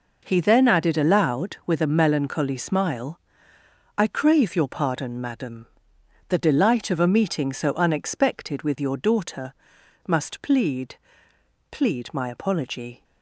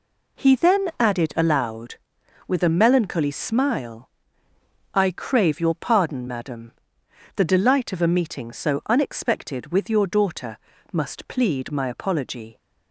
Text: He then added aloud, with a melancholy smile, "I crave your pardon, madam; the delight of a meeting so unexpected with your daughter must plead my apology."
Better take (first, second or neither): second